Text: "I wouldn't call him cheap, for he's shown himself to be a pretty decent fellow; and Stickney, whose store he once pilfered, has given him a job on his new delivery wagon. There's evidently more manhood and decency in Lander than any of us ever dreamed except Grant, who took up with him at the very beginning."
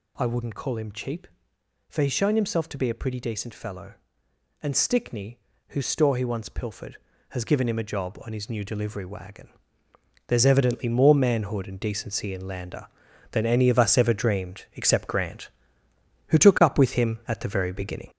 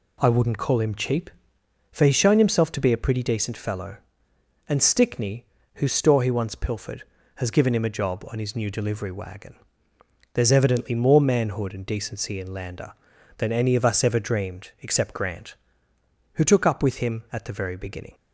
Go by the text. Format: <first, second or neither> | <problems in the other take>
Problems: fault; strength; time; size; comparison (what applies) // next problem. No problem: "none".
second | gets louder; noticeable; throughout; 4.5 dB